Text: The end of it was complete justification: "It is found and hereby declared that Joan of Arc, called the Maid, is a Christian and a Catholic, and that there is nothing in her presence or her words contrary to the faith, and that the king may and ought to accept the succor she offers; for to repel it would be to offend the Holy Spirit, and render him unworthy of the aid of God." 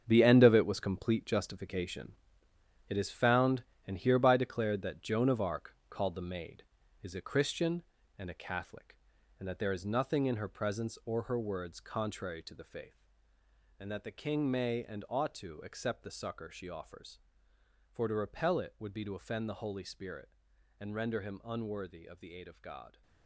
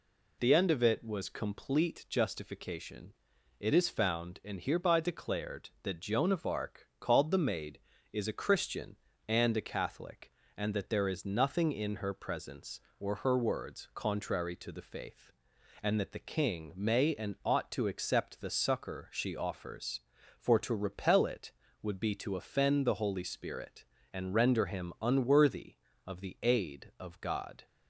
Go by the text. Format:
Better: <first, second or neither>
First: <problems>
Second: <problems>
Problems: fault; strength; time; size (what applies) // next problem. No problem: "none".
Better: second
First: gets quieter; strong; throughout; 11 dB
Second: none